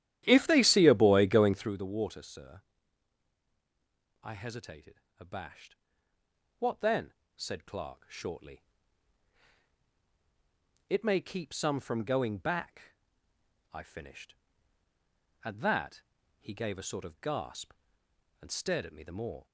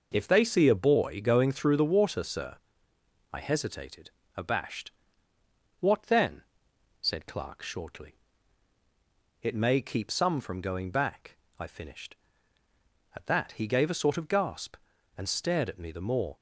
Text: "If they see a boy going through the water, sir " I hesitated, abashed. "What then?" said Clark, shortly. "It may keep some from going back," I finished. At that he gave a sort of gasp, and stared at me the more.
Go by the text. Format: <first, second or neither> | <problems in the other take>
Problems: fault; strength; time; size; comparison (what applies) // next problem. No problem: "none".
second | starts louder than the rest; strong; until 1.8 s; 12 dB // pauses between "that" and "he"; at 16.0 s; 0.38 s long